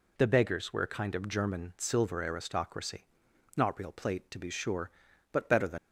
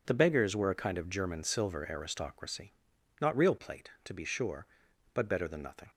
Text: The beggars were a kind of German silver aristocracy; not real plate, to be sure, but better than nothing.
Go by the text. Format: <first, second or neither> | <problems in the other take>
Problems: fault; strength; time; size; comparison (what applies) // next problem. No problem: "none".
second | stops before "nothing"; at 5.7 s